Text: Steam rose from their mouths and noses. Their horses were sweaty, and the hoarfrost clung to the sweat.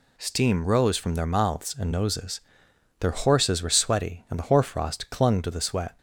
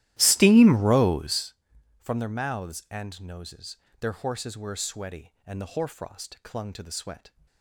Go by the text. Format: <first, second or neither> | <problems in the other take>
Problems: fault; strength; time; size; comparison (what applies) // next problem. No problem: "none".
first | starts louder than the rest; strong; until 1.5 s; 14.5 dB